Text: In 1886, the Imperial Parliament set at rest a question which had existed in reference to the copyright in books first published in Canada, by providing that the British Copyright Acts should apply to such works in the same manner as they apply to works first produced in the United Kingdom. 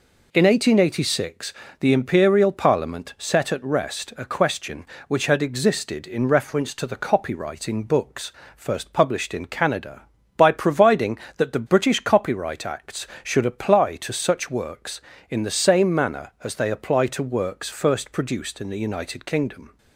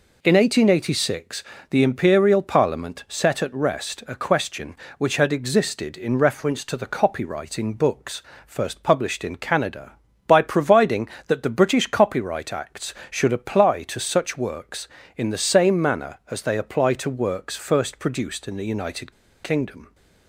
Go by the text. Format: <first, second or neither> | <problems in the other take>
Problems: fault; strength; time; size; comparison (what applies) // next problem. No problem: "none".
first | pauses between "books" and "first"; slight; at 8.2 s; 0.26 s long; slight in the first // pauses between "United" and "Kingdom"; slight; at 19.1 s; 0.31 s long